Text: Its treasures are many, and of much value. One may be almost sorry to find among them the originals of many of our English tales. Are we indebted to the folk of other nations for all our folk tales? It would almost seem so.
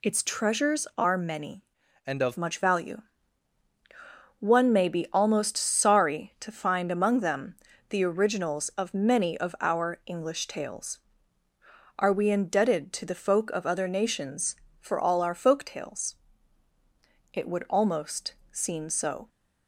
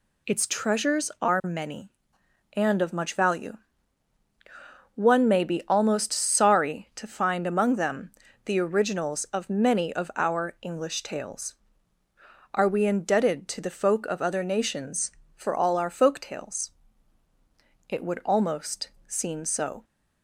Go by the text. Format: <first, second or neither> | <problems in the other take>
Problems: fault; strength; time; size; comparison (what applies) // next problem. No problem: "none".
second | changes voice from "and" to "of"; from 2.0 to 2.3 s; 0.3 s long // pauses between "them" and "the"; slight; at 7.5 s; 0.34 s long; slight in the second // pauses between "almost" and "seem"; slight; at 18.3 s; 0.16 s long; slight in the second